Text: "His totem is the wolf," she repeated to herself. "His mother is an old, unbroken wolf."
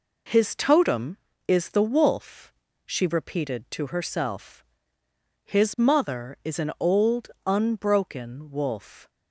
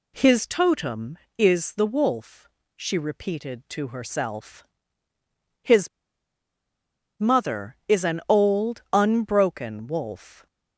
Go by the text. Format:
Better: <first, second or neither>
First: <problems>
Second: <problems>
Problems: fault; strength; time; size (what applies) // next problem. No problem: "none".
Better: first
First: none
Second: pauses between "His" and "mother"; strong; at 5.8 s; 1.3 s long